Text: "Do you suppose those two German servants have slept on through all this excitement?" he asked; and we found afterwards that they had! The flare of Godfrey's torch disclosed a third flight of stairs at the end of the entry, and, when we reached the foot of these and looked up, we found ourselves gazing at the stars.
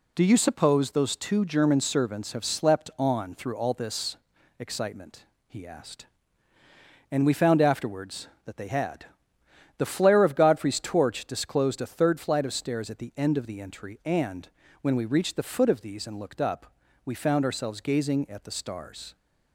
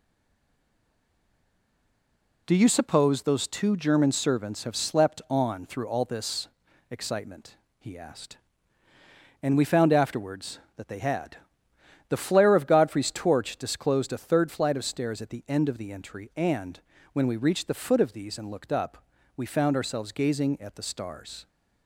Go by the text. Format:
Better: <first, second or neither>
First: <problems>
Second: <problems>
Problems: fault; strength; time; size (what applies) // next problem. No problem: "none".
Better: first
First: pauses between "this" and "excitement"; at 4.1 s; 0.44 s long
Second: stays silent before the first word; until 2.4 s; 2.4 s long // pauses between "this" and "excitement"; at 6.4 s; 0.44 s long